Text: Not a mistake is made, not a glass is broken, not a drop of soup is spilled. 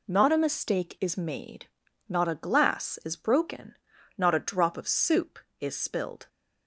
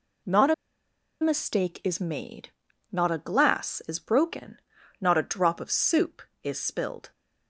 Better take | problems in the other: first | pauses between "a" and "mistake"; noticeable; at 0.5 s; 0.68 s long

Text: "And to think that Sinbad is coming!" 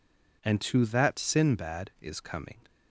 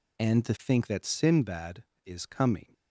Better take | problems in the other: second | skips "think"; at 0.8 s

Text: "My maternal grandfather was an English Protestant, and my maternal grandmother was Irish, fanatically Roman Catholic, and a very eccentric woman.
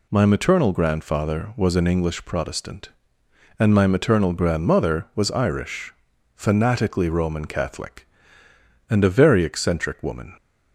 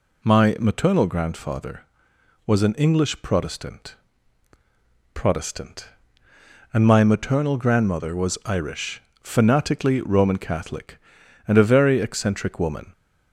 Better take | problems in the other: first | says "Protestant" twice; at 5.1 s

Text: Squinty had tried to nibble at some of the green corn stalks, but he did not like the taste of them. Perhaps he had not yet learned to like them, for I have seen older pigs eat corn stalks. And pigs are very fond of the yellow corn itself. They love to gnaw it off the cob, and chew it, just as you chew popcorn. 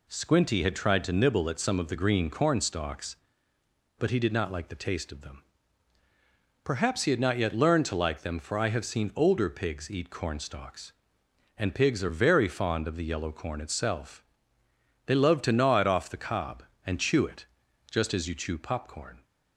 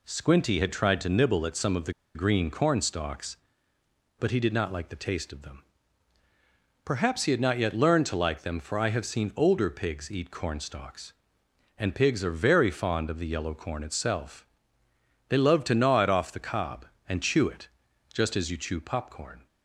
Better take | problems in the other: first | pauses between "the" and "green"; slight; at 1.9 s; 0.22 s long

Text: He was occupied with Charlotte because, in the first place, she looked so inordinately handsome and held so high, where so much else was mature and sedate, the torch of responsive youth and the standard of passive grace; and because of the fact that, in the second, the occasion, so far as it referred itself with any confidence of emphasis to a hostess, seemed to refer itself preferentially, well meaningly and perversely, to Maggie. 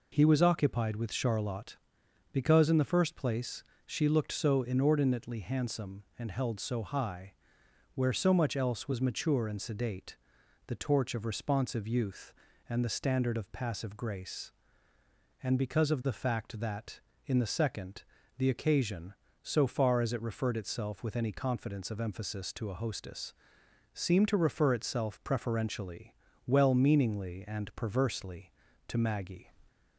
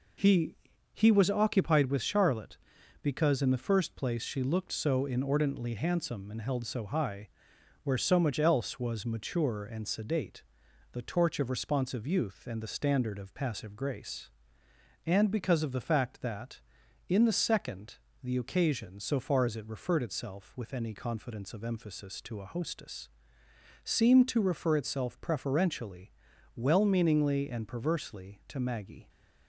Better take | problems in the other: first | says "He" twice; at 0.9 s

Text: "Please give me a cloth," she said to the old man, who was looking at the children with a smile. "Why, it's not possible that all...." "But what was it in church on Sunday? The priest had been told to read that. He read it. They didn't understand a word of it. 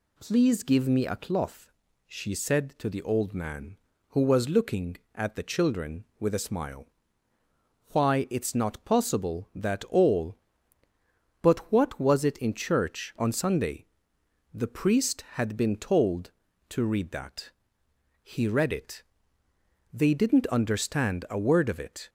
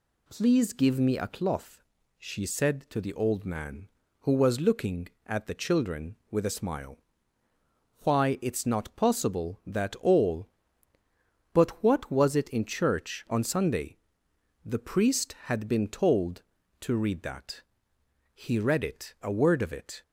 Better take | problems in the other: first | skips "They didn't understand"; at 19.1 s

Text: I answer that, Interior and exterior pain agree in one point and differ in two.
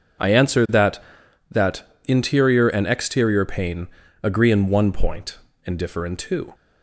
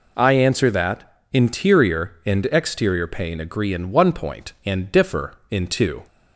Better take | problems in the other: second | says "that" twice; at 1.4 s // pauses between "pain" and "agree"; at 3.8 s; 0.38 s long

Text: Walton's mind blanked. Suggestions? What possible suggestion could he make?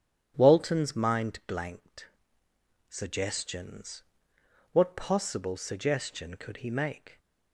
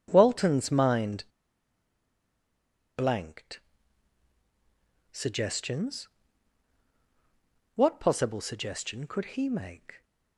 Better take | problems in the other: first | starts louder than the rest; strong; until 1.1 s; 9.5 dB; strong in the first // pauses between "mind" and "blanked"; strong; at 1.2 s; 1.7 s long

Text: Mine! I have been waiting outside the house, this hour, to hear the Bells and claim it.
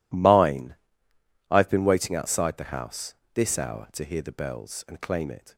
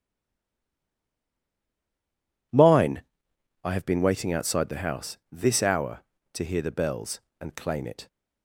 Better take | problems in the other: first | stays silent before the first word; until 2.5 s; 2.5 s long

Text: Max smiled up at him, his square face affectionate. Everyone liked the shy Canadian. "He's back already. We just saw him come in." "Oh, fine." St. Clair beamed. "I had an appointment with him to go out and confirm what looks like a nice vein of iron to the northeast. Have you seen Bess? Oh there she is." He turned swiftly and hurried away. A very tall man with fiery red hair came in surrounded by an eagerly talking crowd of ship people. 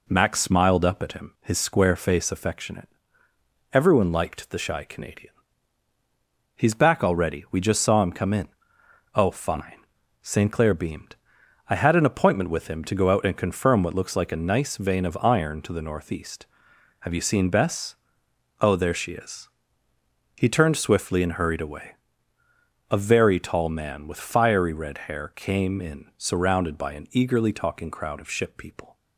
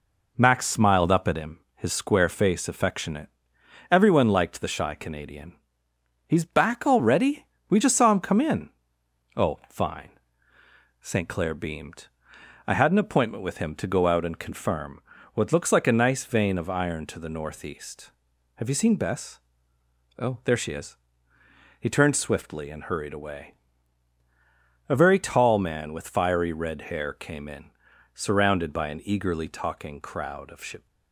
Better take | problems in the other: first | pauses between "confirm" and "what"; slight; at 15.0 s; 0.32 s long // pauses between "in" and "surrounded"; at 27.7 s; 0.42 s long // stops before "people"; at 30.8 s

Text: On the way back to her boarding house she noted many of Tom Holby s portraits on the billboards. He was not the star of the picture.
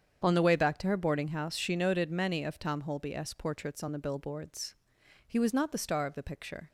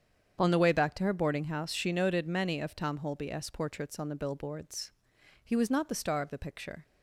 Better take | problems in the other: neither | starts louder than the rest; strong; the same in both

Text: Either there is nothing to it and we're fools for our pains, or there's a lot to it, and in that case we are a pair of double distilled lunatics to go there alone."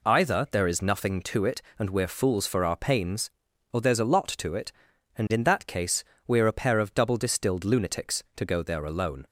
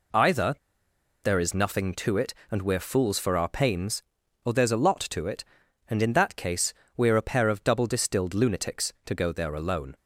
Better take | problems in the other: first | pauses between "Either" and "there"; noticeable; at 0.5 s; 0.67 s long // pauses between "case" and "we"; slight; at 6.7 s; 0.24 s long; slight in the first

